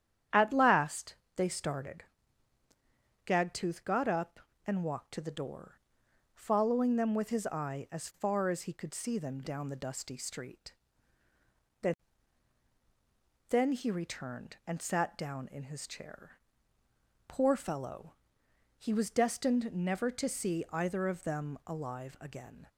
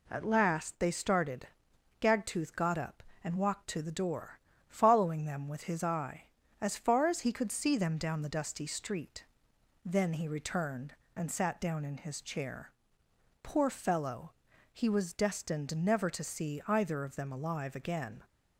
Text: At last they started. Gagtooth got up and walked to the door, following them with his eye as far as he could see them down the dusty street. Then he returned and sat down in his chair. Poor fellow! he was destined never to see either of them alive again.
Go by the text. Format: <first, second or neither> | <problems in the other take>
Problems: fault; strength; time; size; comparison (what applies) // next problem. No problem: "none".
second | starts louder than the rest; strong; until 1.5 s; 10 dB // pauses between "last" and "they"; slight; at 1.1 s; 0.22 s long // says "Then" twice; at 13.4 s